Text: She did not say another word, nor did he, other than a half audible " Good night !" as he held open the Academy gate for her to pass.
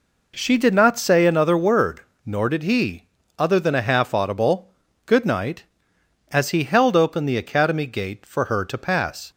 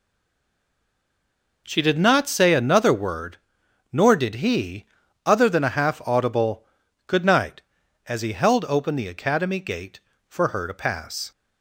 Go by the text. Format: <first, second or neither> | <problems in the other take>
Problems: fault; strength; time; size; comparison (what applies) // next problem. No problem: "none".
first | stays silent before the first word; noticeable; until 1.6 s; 1.6 s long